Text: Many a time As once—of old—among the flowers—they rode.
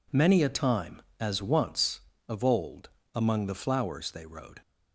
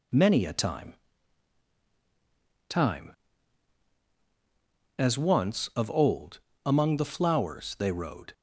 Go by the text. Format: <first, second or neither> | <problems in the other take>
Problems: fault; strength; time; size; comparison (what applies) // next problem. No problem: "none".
first | says "time" twice; at 2.6 s